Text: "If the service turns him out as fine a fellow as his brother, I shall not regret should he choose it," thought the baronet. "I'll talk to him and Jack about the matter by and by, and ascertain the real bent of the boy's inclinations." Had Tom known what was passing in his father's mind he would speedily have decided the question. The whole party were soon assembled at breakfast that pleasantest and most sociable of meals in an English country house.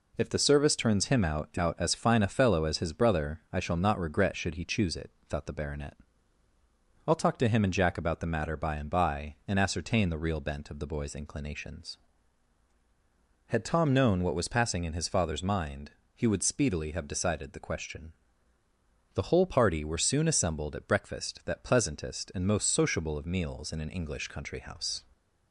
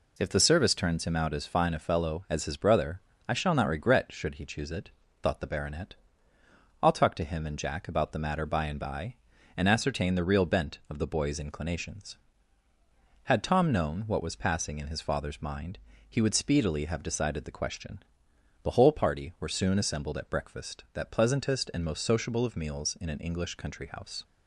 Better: second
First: says "out" twice; at 1.5 s // pauses between "mind" and "he"; slight; at 15.8 s; 0.24 s long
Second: pauses between "mind" and "he"; slight; at 15.7 s; 0.32 s long

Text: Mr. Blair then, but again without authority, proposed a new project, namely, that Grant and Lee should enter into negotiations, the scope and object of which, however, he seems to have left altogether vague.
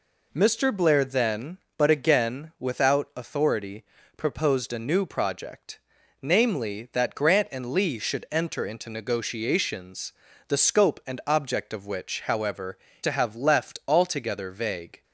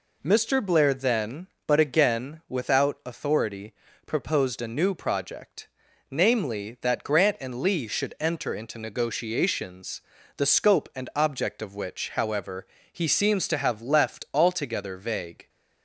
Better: second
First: skips "he seems"; at 12.9 s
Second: none

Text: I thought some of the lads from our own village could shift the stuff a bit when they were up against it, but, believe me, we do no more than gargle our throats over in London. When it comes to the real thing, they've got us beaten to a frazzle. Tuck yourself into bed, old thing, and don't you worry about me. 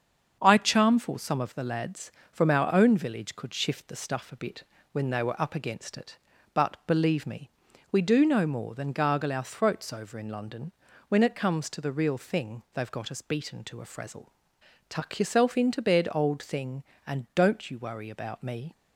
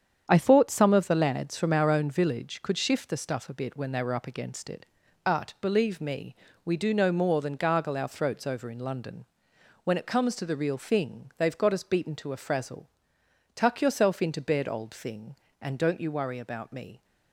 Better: second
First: starts louder than the rest; until 1.4 s; 7 dB // says "charmful" for "thought"; at 0.5 s // pauses between "bit" and "when"; slight; at 4.6 s; 0.30 s long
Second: starts louder than the rest; strong; until 1.3 s; 8 dB

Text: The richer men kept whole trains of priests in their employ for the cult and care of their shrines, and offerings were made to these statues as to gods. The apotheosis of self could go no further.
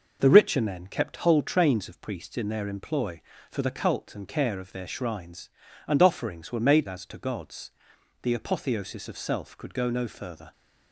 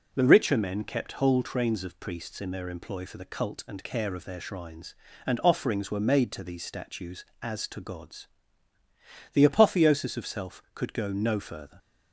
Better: second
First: skips "to these statues"; at 6.8 s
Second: none

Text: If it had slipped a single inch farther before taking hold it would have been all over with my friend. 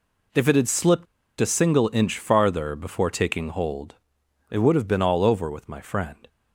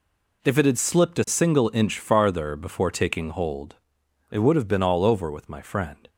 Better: second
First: pauses between "slipped" and "a"; slight; at 1.0 s; 0.34 s long // pauses between "hold" and "it"; noticeable; at 3.9 s; 0.52 s long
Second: pauses between "hold" and "it"; noticeable; at 3.7 s; 0.52 s long

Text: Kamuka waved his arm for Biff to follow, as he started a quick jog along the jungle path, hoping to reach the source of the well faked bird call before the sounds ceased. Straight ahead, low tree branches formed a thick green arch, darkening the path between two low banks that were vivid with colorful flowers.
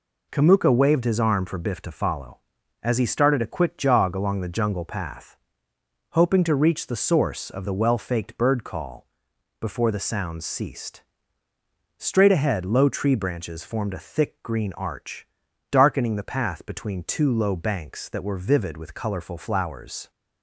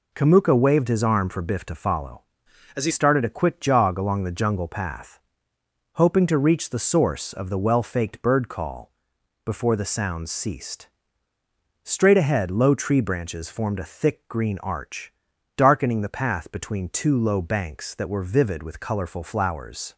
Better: first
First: pauses between "call" and "before"; noticeable; at 9.0 s; 0.54 s long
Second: changes voice from "as" to "he"; from 2.7 to 2.9 s; 0.2 s long // pauses between "call" and "before"; noticeable; at 8.9 s; 0.54 s long

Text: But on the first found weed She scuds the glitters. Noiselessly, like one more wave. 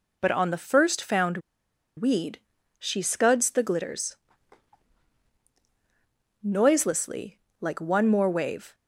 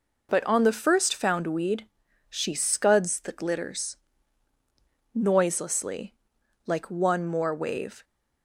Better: second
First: pauses between "found" and "weed"; noticeable; at 1.3 s; 0.58 s long // pauses between "weed" and "She"; at 2.3 s; 0.40 s long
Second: pauses between "weed" and "She"; at 1.8 s; 0.42 s long

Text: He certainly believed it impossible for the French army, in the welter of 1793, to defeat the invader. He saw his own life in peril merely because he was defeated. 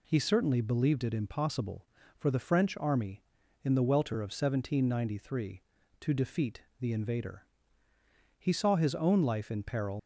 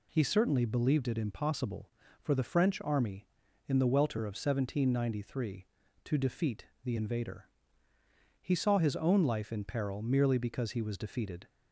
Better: second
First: pauses between "defeat" and "the"; slight; at 6.6 s; 0.18 s long // stops before "merely because he was defeated"; at 9.9 s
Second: pauses between "defeat" and "the"; slight; at 6.6 s; 0.18 s long

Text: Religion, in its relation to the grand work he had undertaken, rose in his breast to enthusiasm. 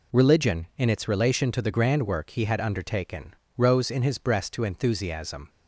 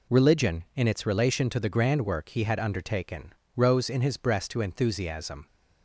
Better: neither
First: none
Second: none

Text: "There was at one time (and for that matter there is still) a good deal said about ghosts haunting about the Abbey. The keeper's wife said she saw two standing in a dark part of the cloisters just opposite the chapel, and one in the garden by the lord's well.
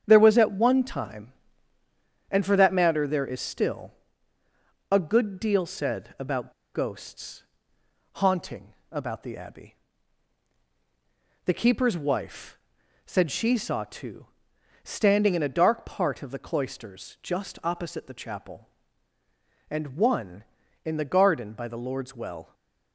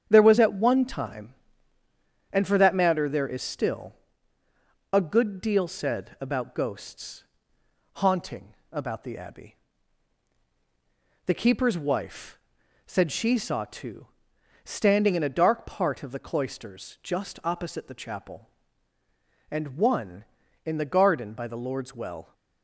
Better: second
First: starts louder than the rest; strong; until 1.0 s; 8.5 dB // pauses between "about" and "ghosts"; slight; at 6.5 s; 0.22 s long // pauses between "ghosts" and "haunting"; noticeable; at 7.4 s; 0.74 s long // pauses between "haunting" and "about"; slight; at 8.7 s; 0.18 s long // pauses between "wife" and "said"; at 12.5 s; 0.44 s long // pauses between "two" and "standing"; noticeable; at 14.2 s; 0.56 s long // stays silent after the last word; slight; from 22.4 s on; 0.5 s long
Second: starts louder than the rest; strong; until 1.1 s; 8 dB // pauses between "ghosts" and "haunting"; noticeable; at 7.2 s; 0.74 s long // pauses between "haunting" and "about"; slight; at 8.5 s; 0.18 s long // pauses between "wife" and "said"; at 12.3 s; 0.44 s long // pauses between "two" and "standing"; noticeable; at 14.0 s; 0.56 s long

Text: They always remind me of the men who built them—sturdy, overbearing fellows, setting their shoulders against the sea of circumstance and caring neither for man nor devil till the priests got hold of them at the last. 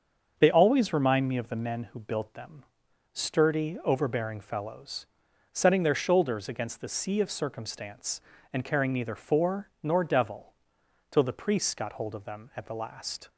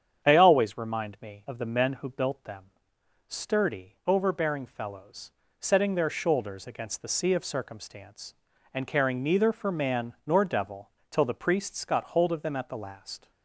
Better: second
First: starts louder than the rest; until 1.3 s; 7 dB // skips "man"; at 9.7 s // pauses between "devil" and "till"; noticeable; at 10.5 s; 0.58 s long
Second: starts louder than the rest; strong; until 1.3 s; 8 dB // pauses between "devil" and "till"; slight; at 10.9 s; 0.20 s long

